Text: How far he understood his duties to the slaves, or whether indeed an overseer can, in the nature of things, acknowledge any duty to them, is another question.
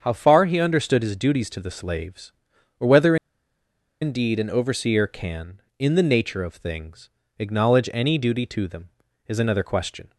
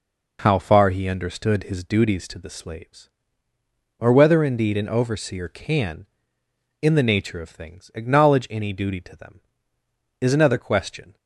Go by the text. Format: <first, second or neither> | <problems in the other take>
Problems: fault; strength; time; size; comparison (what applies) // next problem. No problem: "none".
second | starts louder than the rest; strong; until 1.0 s; 7 dB // pauses between "whether" and "indeed"; noticeable; at 3.1 s; 0.86 s long